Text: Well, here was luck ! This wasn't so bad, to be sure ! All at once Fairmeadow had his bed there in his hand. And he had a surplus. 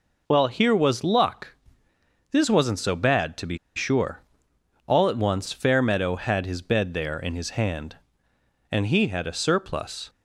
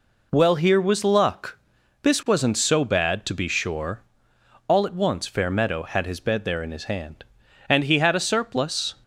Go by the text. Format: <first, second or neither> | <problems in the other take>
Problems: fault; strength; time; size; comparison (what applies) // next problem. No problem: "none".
second | pauses between "be" and "sure"; slight; at 3.5 s; 0.18 s long